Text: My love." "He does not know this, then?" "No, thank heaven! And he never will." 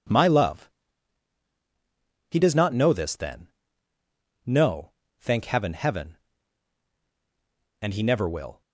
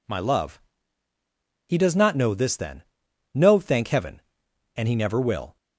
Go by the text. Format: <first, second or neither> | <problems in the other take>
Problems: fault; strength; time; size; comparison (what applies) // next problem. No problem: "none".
second | says "heaven" twice; at 5.7 s